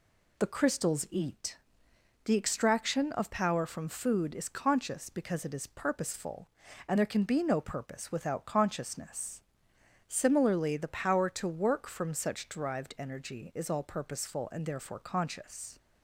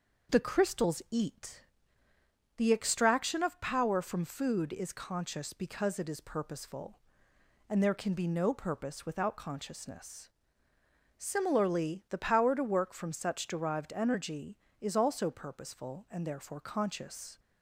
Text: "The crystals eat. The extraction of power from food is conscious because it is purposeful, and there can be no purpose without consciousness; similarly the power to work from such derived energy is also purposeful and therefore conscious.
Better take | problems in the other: second | says "all" for "also"; at 13.6 s

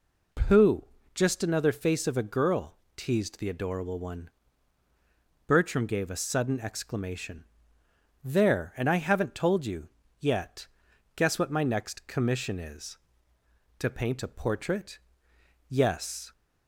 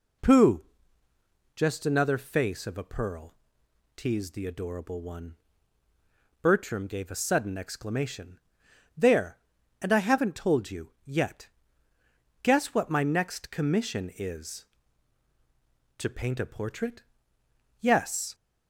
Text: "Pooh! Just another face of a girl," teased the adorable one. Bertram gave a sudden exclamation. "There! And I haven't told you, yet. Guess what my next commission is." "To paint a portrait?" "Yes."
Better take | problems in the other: first | says "pearl" for "girl"; at 2.8 s

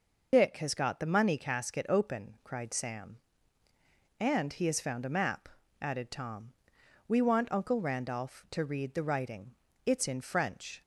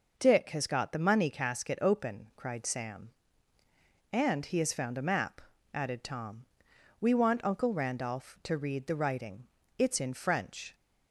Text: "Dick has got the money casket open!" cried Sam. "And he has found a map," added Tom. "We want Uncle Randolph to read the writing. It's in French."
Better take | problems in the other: second | loses the start of "Dick"; at 0.3 s; 70 ms

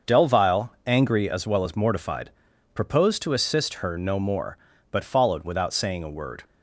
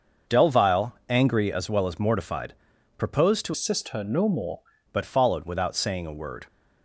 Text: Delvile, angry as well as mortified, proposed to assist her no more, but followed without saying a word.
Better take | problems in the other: first | starts louder than the rest; until 1.4 s; 6.5 dB; also in the first // changes voice from "assist" to "more"; from 3.5 to 4.6 s; 1.1 s long

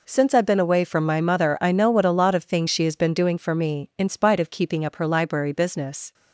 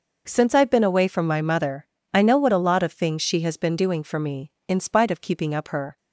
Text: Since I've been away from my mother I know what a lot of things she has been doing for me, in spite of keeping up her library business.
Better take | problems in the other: first | pauses between "mother" and "I"; slight; at 1.8 s; 0.26 s long // stops before "library business"; at 5.9 s

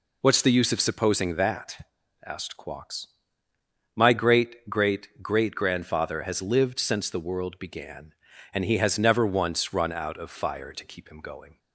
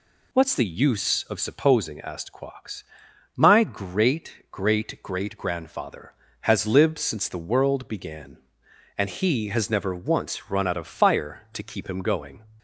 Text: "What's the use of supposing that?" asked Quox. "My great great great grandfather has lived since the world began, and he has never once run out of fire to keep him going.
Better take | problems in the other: first | skips "that"; at 1.9 s

